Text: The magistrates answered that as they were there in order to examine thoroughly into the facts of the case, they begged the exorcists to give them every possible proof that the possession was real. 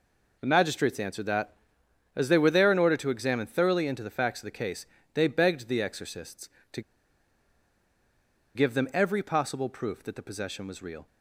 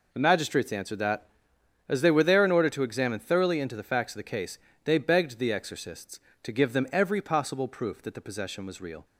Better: second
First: pauses between "to" and "give"; strong; at 6.8 s; 1.7 s long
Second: none

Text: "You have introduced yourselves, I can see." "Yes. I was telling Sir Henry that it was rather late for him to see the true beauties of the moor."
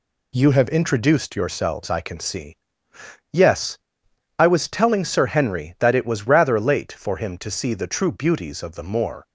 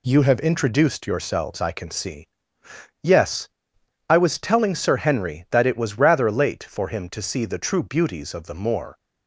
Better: neither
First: none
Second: none

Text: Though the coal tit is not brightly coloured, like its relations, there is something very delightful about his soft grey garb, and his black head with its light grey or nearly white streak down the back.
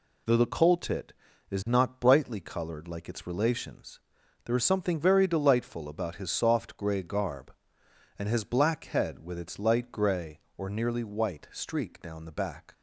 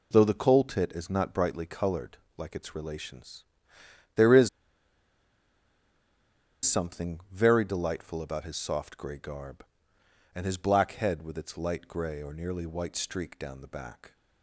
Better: first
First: none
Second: pauses between "is" and "something"; strong; at 4.4 s; 2.1 s long

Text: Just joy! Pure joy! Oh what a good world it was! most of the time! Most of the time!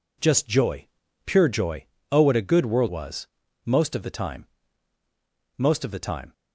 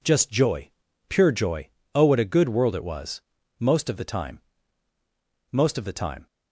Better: second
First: skips "it"; at 2.8 s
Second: none

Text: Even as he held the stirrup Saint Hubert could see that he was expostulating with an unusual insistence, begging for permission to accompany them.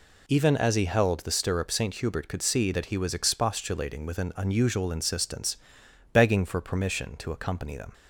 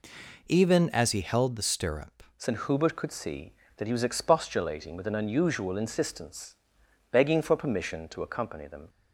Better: first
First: none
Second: changes voice at "Saint"; from 2.3 s on; 6.5 s long

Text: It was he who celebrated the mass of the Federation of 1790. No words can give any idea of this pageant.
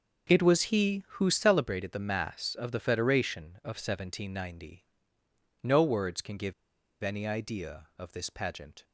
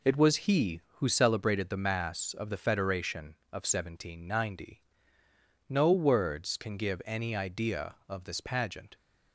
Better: second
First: pauses between "give" and "any"; noticeable; at 6.5 s; 0.48 s long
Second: none

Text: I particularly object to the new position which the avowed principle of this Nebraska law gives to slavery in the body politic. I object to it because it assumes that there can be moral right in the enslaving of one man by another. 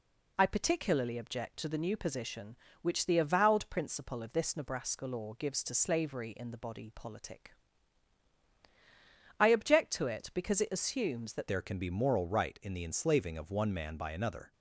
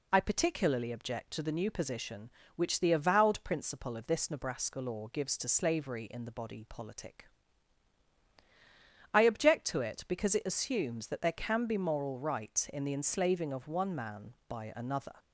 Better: second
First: changes voice at "there"; from 11.4 s on; 3.1 s long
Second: none

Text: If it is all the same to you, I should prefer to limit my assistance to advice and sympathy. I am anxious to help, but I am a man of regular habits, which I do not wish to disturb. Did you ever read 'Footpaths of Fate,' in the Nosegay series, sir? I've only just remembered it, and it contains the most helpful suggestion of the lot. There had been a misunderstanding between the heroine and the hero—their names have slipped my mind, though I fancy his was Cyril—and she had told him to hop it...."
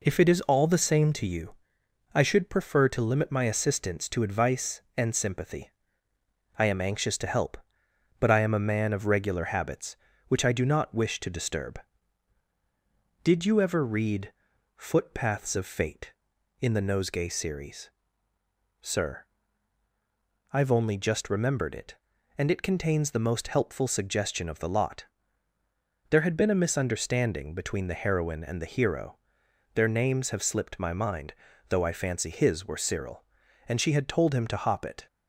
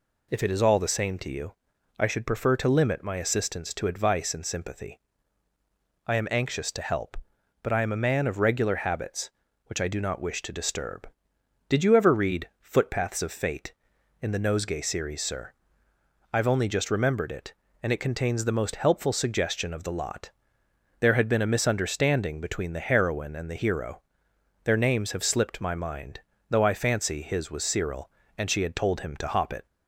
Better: second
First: pauses between "read" and "Footpaths"; at 14.3 s; 0.42 s long // says "were" for "was"; at 32.6 s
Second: none

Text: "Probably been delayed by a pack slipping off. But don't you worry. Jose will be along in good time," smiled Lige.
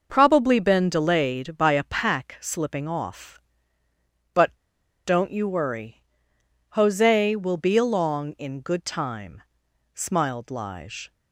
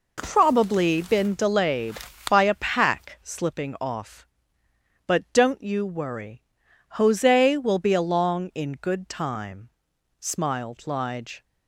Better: second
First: pauses between "But" and "don't"; noticeable; at 4.5 s; 0.53 s long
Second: none

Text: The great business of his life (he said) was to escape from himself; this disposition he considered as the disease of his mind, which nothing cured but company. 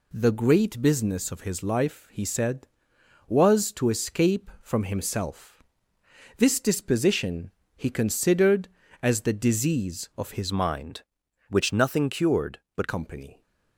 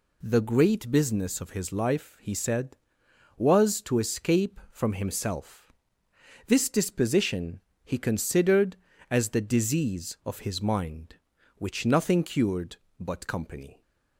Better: second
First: pauses between "disposition" and "he"; slight; at 7.4 s; 0.28 s long // changes voice from "mind" to "but"; from 10.5 to 12.8 s; 2.3 s long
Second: pauses between "disposition" and "he"; slight; at 7.5 s; 0.26 s long

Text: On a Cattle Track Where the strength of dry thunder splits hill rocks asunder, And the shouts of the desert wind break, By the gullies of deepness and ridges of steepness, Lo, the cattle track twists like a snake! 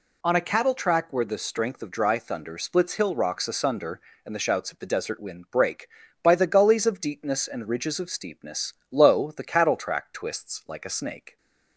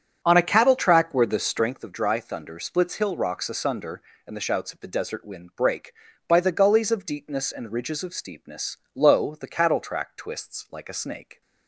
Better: first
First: none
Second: starts louder than the rest; strong; until 1.7 s; 8.5 dB

